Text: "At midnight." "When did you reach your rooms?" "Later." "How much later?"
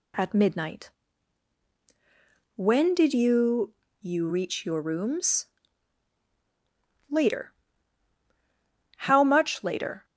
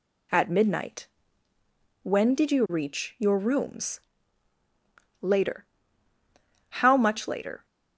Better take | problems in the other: second | says "you" twice; at 4.0 s

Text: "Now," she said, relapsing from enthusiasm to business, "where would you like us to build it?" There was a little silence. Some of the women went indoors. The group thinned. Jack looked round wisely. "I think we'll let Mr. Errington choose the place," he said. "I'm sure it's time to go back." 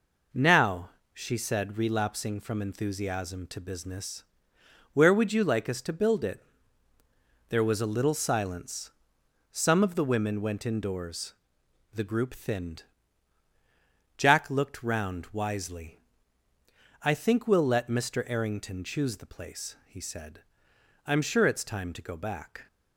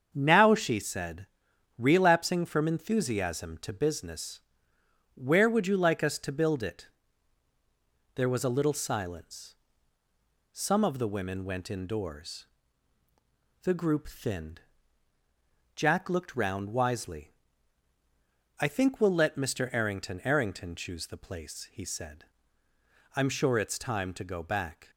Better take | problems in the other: first | starts louder than the rest; strong; until 1.1 s; 7 dB // says "Errington" twice; at 20.2 s

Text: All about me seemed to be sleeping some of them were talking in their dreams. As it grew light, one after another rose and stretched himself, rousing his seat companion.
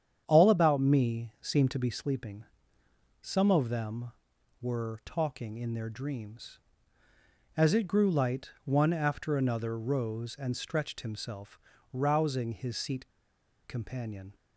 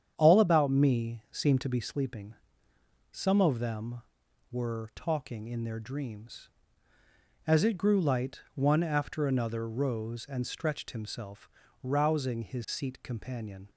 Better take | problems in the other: second | starts louder than the rest; strong; until 1.2 s; 8.5 dB; strong in the second // pauses between "sleeping" and "some"; noticeable; at 2.4 s; 0.76 s long; noticeable in the second // pauses between "seat" and "companion"; noticeable; at 13.0 s; 0.58 s long

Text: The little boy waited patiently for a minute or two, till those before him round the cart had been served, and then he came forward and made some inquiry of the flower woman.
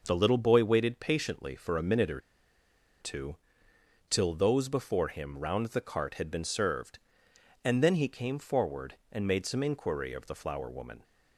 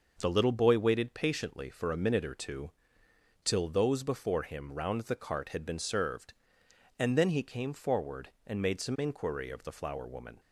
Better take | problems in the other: second | pauses between "or" and "two"; noticeable; at 2.1 s; 0.82 s long

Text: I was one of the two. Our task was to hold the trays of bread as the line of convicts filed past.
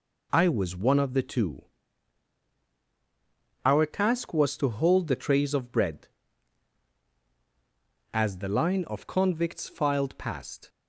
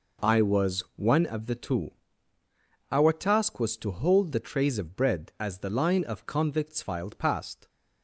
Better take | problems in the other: neither | none

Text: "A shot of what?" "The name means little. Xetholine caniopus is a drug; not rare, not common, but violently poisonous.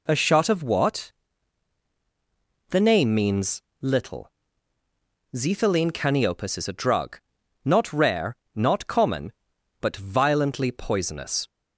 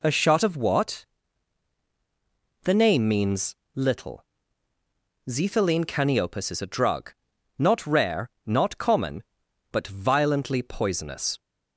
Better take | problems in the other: neither | pauses between "means" and "little"; slight; the same in both

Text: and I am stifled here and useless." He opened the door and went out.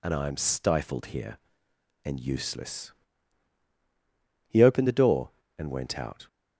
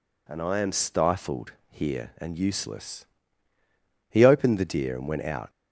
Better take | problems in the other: first | pauses between "stifled" and "here"; slight; at 1.5 s; 0.18 s long // says "deer" for "door"; at 4.6 s

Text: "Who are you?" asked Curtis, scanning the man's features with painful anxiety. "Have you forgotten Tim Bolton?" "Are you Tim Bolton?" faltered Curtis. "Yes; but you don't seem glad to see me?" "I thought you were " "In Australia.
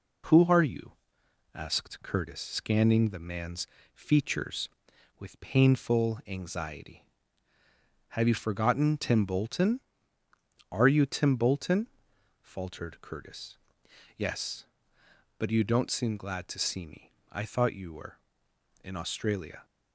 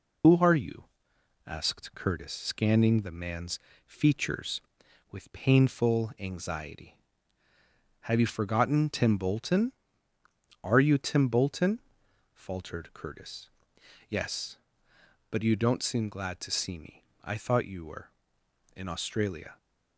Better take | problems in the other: first | loses the start of "Who"; at 0.2 s; 90 ms // pauses between "man's" and "features"; slight; at 3.5 s; 0.26 s long; slight in the first

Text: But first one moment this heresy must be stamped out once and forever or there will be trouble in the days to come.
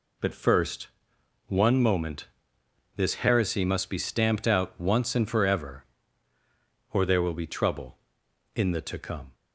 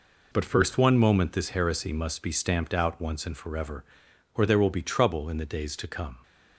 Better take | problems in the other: second | pauses between "first" and "one"; noticeable; at 0.8 s; 0.58 s long // pauses between "moment" and "this"; noticeable; at 2.2 s; 0.70 s long // skips "days"; at 8.8 s

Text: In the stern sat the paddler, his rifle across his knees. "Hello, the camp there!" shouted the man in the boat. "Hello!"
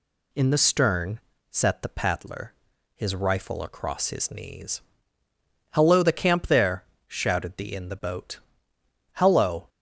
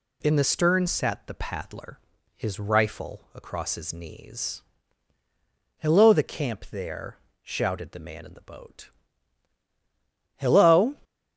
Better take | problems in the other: second | pauses between "stern" and "sat"; slight; at 1.1 s; 0.30 s long // skips "man"; at 7.7 s

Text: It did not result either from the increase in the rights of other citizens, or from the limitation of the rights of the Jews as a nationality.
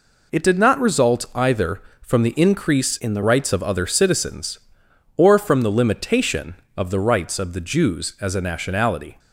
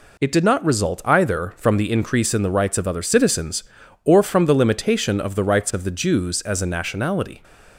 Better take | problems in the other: second | changes voice from "in" to "the"; from 2.9 to 3.2 s; 0.3 s long

